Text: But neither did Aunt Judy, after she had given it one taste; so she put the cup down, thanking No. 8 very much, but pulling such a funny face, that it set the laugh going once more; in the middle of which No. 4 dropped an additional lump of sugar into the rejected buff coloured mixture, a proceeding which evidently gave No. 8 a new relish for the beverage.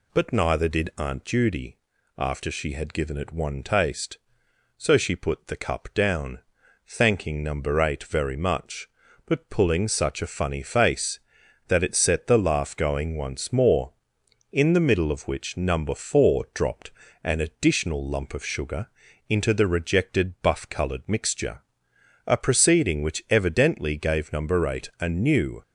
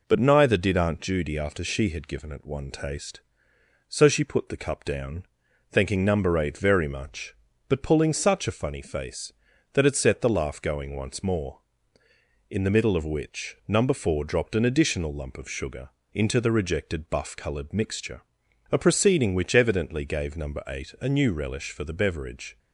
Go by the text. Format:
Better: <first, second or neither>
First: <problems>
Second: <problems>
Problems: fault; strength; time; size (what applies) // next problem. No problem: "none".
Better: second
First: pauses between "dropped" and "an"; slight; at 16.8 s; 0.32 s long // pauses between "sugar" and "into"; at 18.8 s; 0.40 s long // stops before "relish for the beverage"; at 25.6 s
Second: pauses between "sugar" and "into"; slight; at 15.8 s; 0.24 s long